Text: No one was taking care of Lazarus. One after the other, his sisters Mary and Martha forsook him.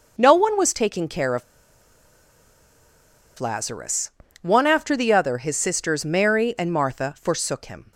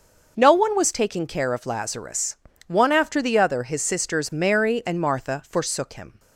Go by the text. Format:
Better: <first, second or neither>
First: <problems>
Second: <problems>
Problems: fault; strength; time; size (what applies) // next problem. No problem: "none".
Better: second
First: pauses between "of" and "Lazarus"; strong; at 1.4 s; 1.9 s long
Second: none